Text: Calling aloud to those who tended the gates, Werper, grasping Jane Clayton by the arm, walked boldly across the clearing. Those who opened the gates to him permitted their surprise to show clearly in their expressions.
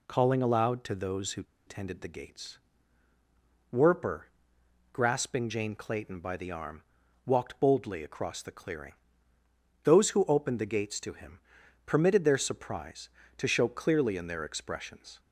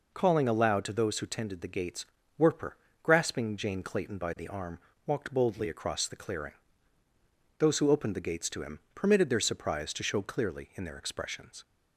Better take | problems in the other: second | pauses between "who" and "tended"; slight; at 1.4 s; 0.23 s long // pauses between "him" and "permitted"; noticeable; at 11.3 s; 0.48 s long; slight in the second

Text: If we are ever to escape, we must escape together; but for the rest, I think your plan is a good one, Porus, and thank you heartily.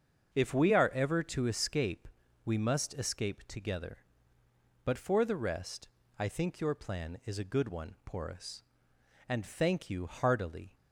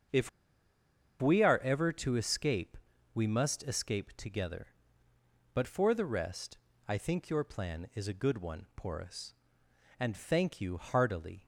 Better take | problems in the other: first | starts louder than the rest; until 2.0 s; 6.5 dB; also in the first // pauses between "If" and "we"; noticeable; at 0.2 s; 0.91 s long

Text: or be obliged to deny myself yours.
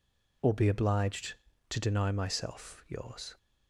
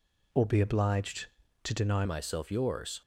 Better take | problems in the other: first | changes voice at "myself"; from 2.0 s on; 1.0 s long

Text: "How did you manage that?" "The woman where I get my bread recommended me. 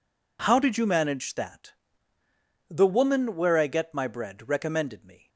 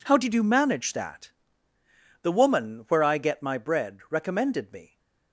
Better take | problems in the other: neither | none

